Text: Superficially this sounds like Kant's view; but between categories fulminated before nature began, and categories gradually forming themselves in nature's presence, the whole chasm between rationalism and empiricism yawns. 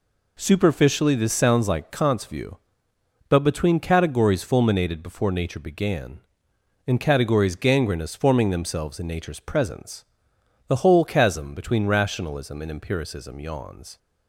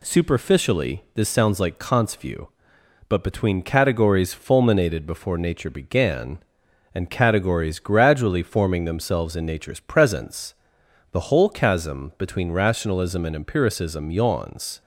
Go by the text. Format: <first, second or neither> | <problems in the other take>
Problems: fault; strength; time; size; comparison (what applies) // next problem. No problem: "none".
second | says "gangrenous" for "gradually"; at 7.5 s